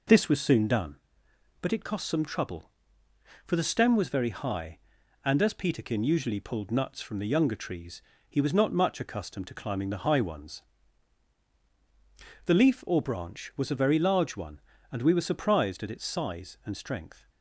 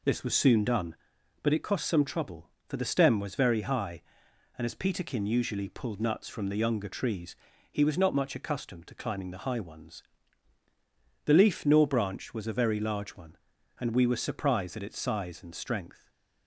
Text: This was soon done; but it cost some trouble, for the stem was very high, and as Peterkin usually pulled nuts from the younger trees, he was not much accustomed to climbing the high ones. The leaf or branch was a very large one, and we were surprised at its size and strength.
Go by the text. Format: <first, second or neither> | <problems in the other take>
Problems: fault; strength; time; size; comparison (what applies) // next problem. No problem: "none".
first | says "nor" for "or"; at 11.6 s // stays silent after the last word; slight; from 15.9 s on; 0.5 s long